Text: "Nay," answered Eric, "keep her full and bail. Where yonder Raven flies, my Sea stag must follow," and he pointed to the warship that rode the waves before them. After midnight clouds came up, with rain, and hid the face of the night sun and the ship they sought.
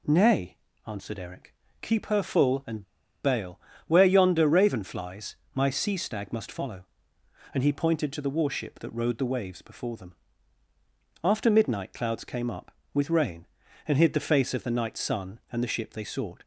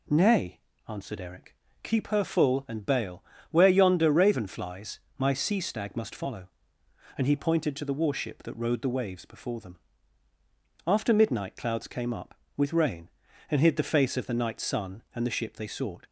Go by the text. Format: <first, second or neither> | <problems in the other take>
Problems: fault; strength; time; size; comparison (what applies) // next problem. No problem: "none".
second | pauses between "and" and "bail"; at 2.8 s; 0.39 s long